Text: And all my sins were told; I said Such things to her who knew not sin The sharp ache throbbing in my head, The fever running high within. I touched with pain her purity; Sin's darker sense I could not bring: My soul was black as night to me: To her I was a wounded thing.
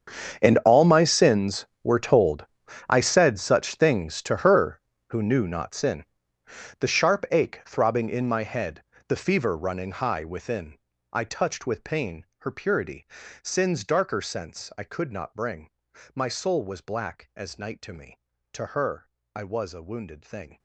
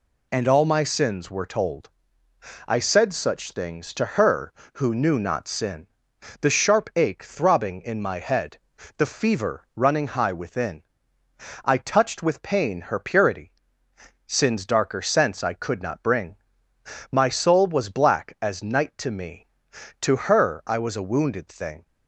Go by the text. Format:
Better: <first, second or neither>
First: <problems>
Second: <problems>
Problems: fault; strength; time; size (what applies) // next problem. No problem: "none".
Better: second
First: gets quieter; strong; throughout; 19 dB // pauses between "sin" and "The"; noticeable; at 6.0 s; 0.76 s long // pauses between "her" and "I"; slight; at 19.1 s; 0.24 s long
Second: pauses between "sin" and "The"; noticeable; at 5.8 s; 0.56 s long